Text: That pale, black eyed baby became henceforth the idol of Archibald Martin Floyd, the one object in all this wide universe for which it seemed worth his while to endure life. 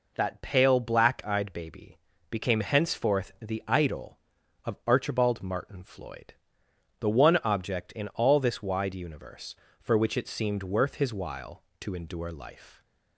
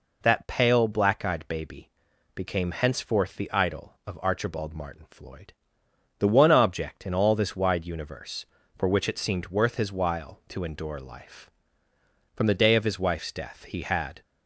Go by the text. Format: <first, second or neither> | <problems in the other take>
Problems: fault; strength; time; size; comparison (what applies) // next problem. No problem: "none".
first | pauses between "baby" and "became"; noticeable; at 1.8 s; 0.46 s long; slight in the first // goes on to say "From the day of his wife's death he had"; strong; from 12.3 s on; 1.8 s long